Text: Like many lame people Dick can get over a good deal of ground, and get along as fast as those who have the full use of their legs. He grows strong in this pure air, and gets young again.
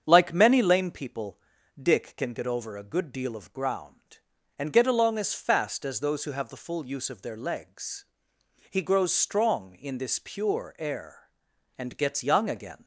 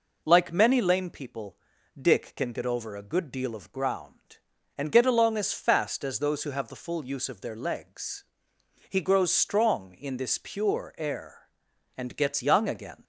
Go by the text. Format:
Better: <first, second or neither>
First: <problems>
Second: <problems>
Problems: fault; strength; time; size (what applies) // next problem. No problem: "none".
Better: second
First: starts louder than the rest; strong; until 1.8 s; 7.5 dB // pauses between "people" and "Dick"; at 1.3 s; 0.42 s long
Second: pauses between "people" and "Dick"; at 1.5 s; 0.42 s long